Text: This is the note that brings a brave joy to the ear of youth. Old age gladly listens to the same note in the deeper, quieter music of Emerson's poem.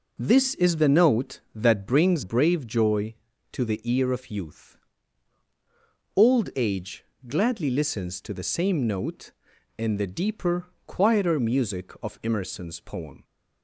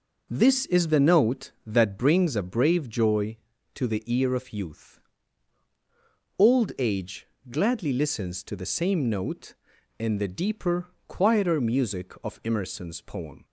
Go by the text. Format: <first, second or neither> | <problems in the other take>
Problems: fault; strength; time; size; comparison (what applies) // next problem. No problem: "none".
second | skips "a"; at 2.2 s // pauses between "age" and "gladly"; slight; at 7.0 s; 0.20 s long; slight in the second